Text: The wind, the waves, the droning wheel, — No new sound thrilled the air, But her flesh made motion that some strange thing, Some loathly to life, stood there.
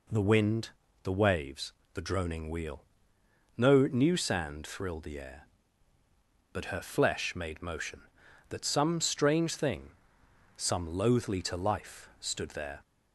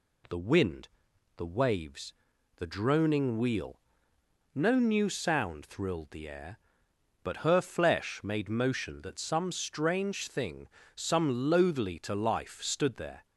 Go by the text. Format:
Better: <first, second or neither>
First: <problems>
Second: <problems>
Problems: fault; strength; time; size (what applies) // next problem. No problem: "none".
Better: second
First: says "sand" for "sound"; at 4.1 s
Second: none